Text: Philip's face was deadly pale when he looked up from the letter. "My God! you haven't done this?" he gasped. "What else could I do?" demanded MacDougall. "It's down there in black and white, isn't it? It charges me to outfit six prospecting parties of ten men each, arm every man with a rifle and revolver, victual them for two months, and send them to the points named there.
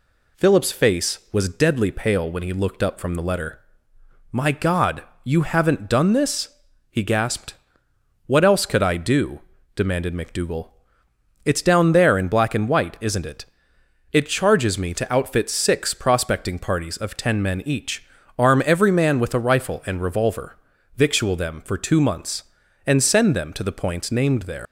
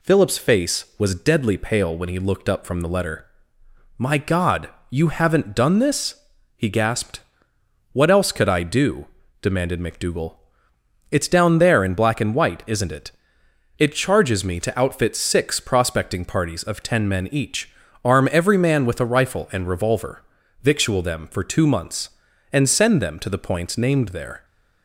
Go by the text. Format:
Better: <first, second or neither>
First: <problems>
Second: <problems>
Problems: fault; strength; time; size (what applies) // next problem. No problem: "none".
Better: second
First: leaves "there" unfinished; at 24.6 s; 130 ms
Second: none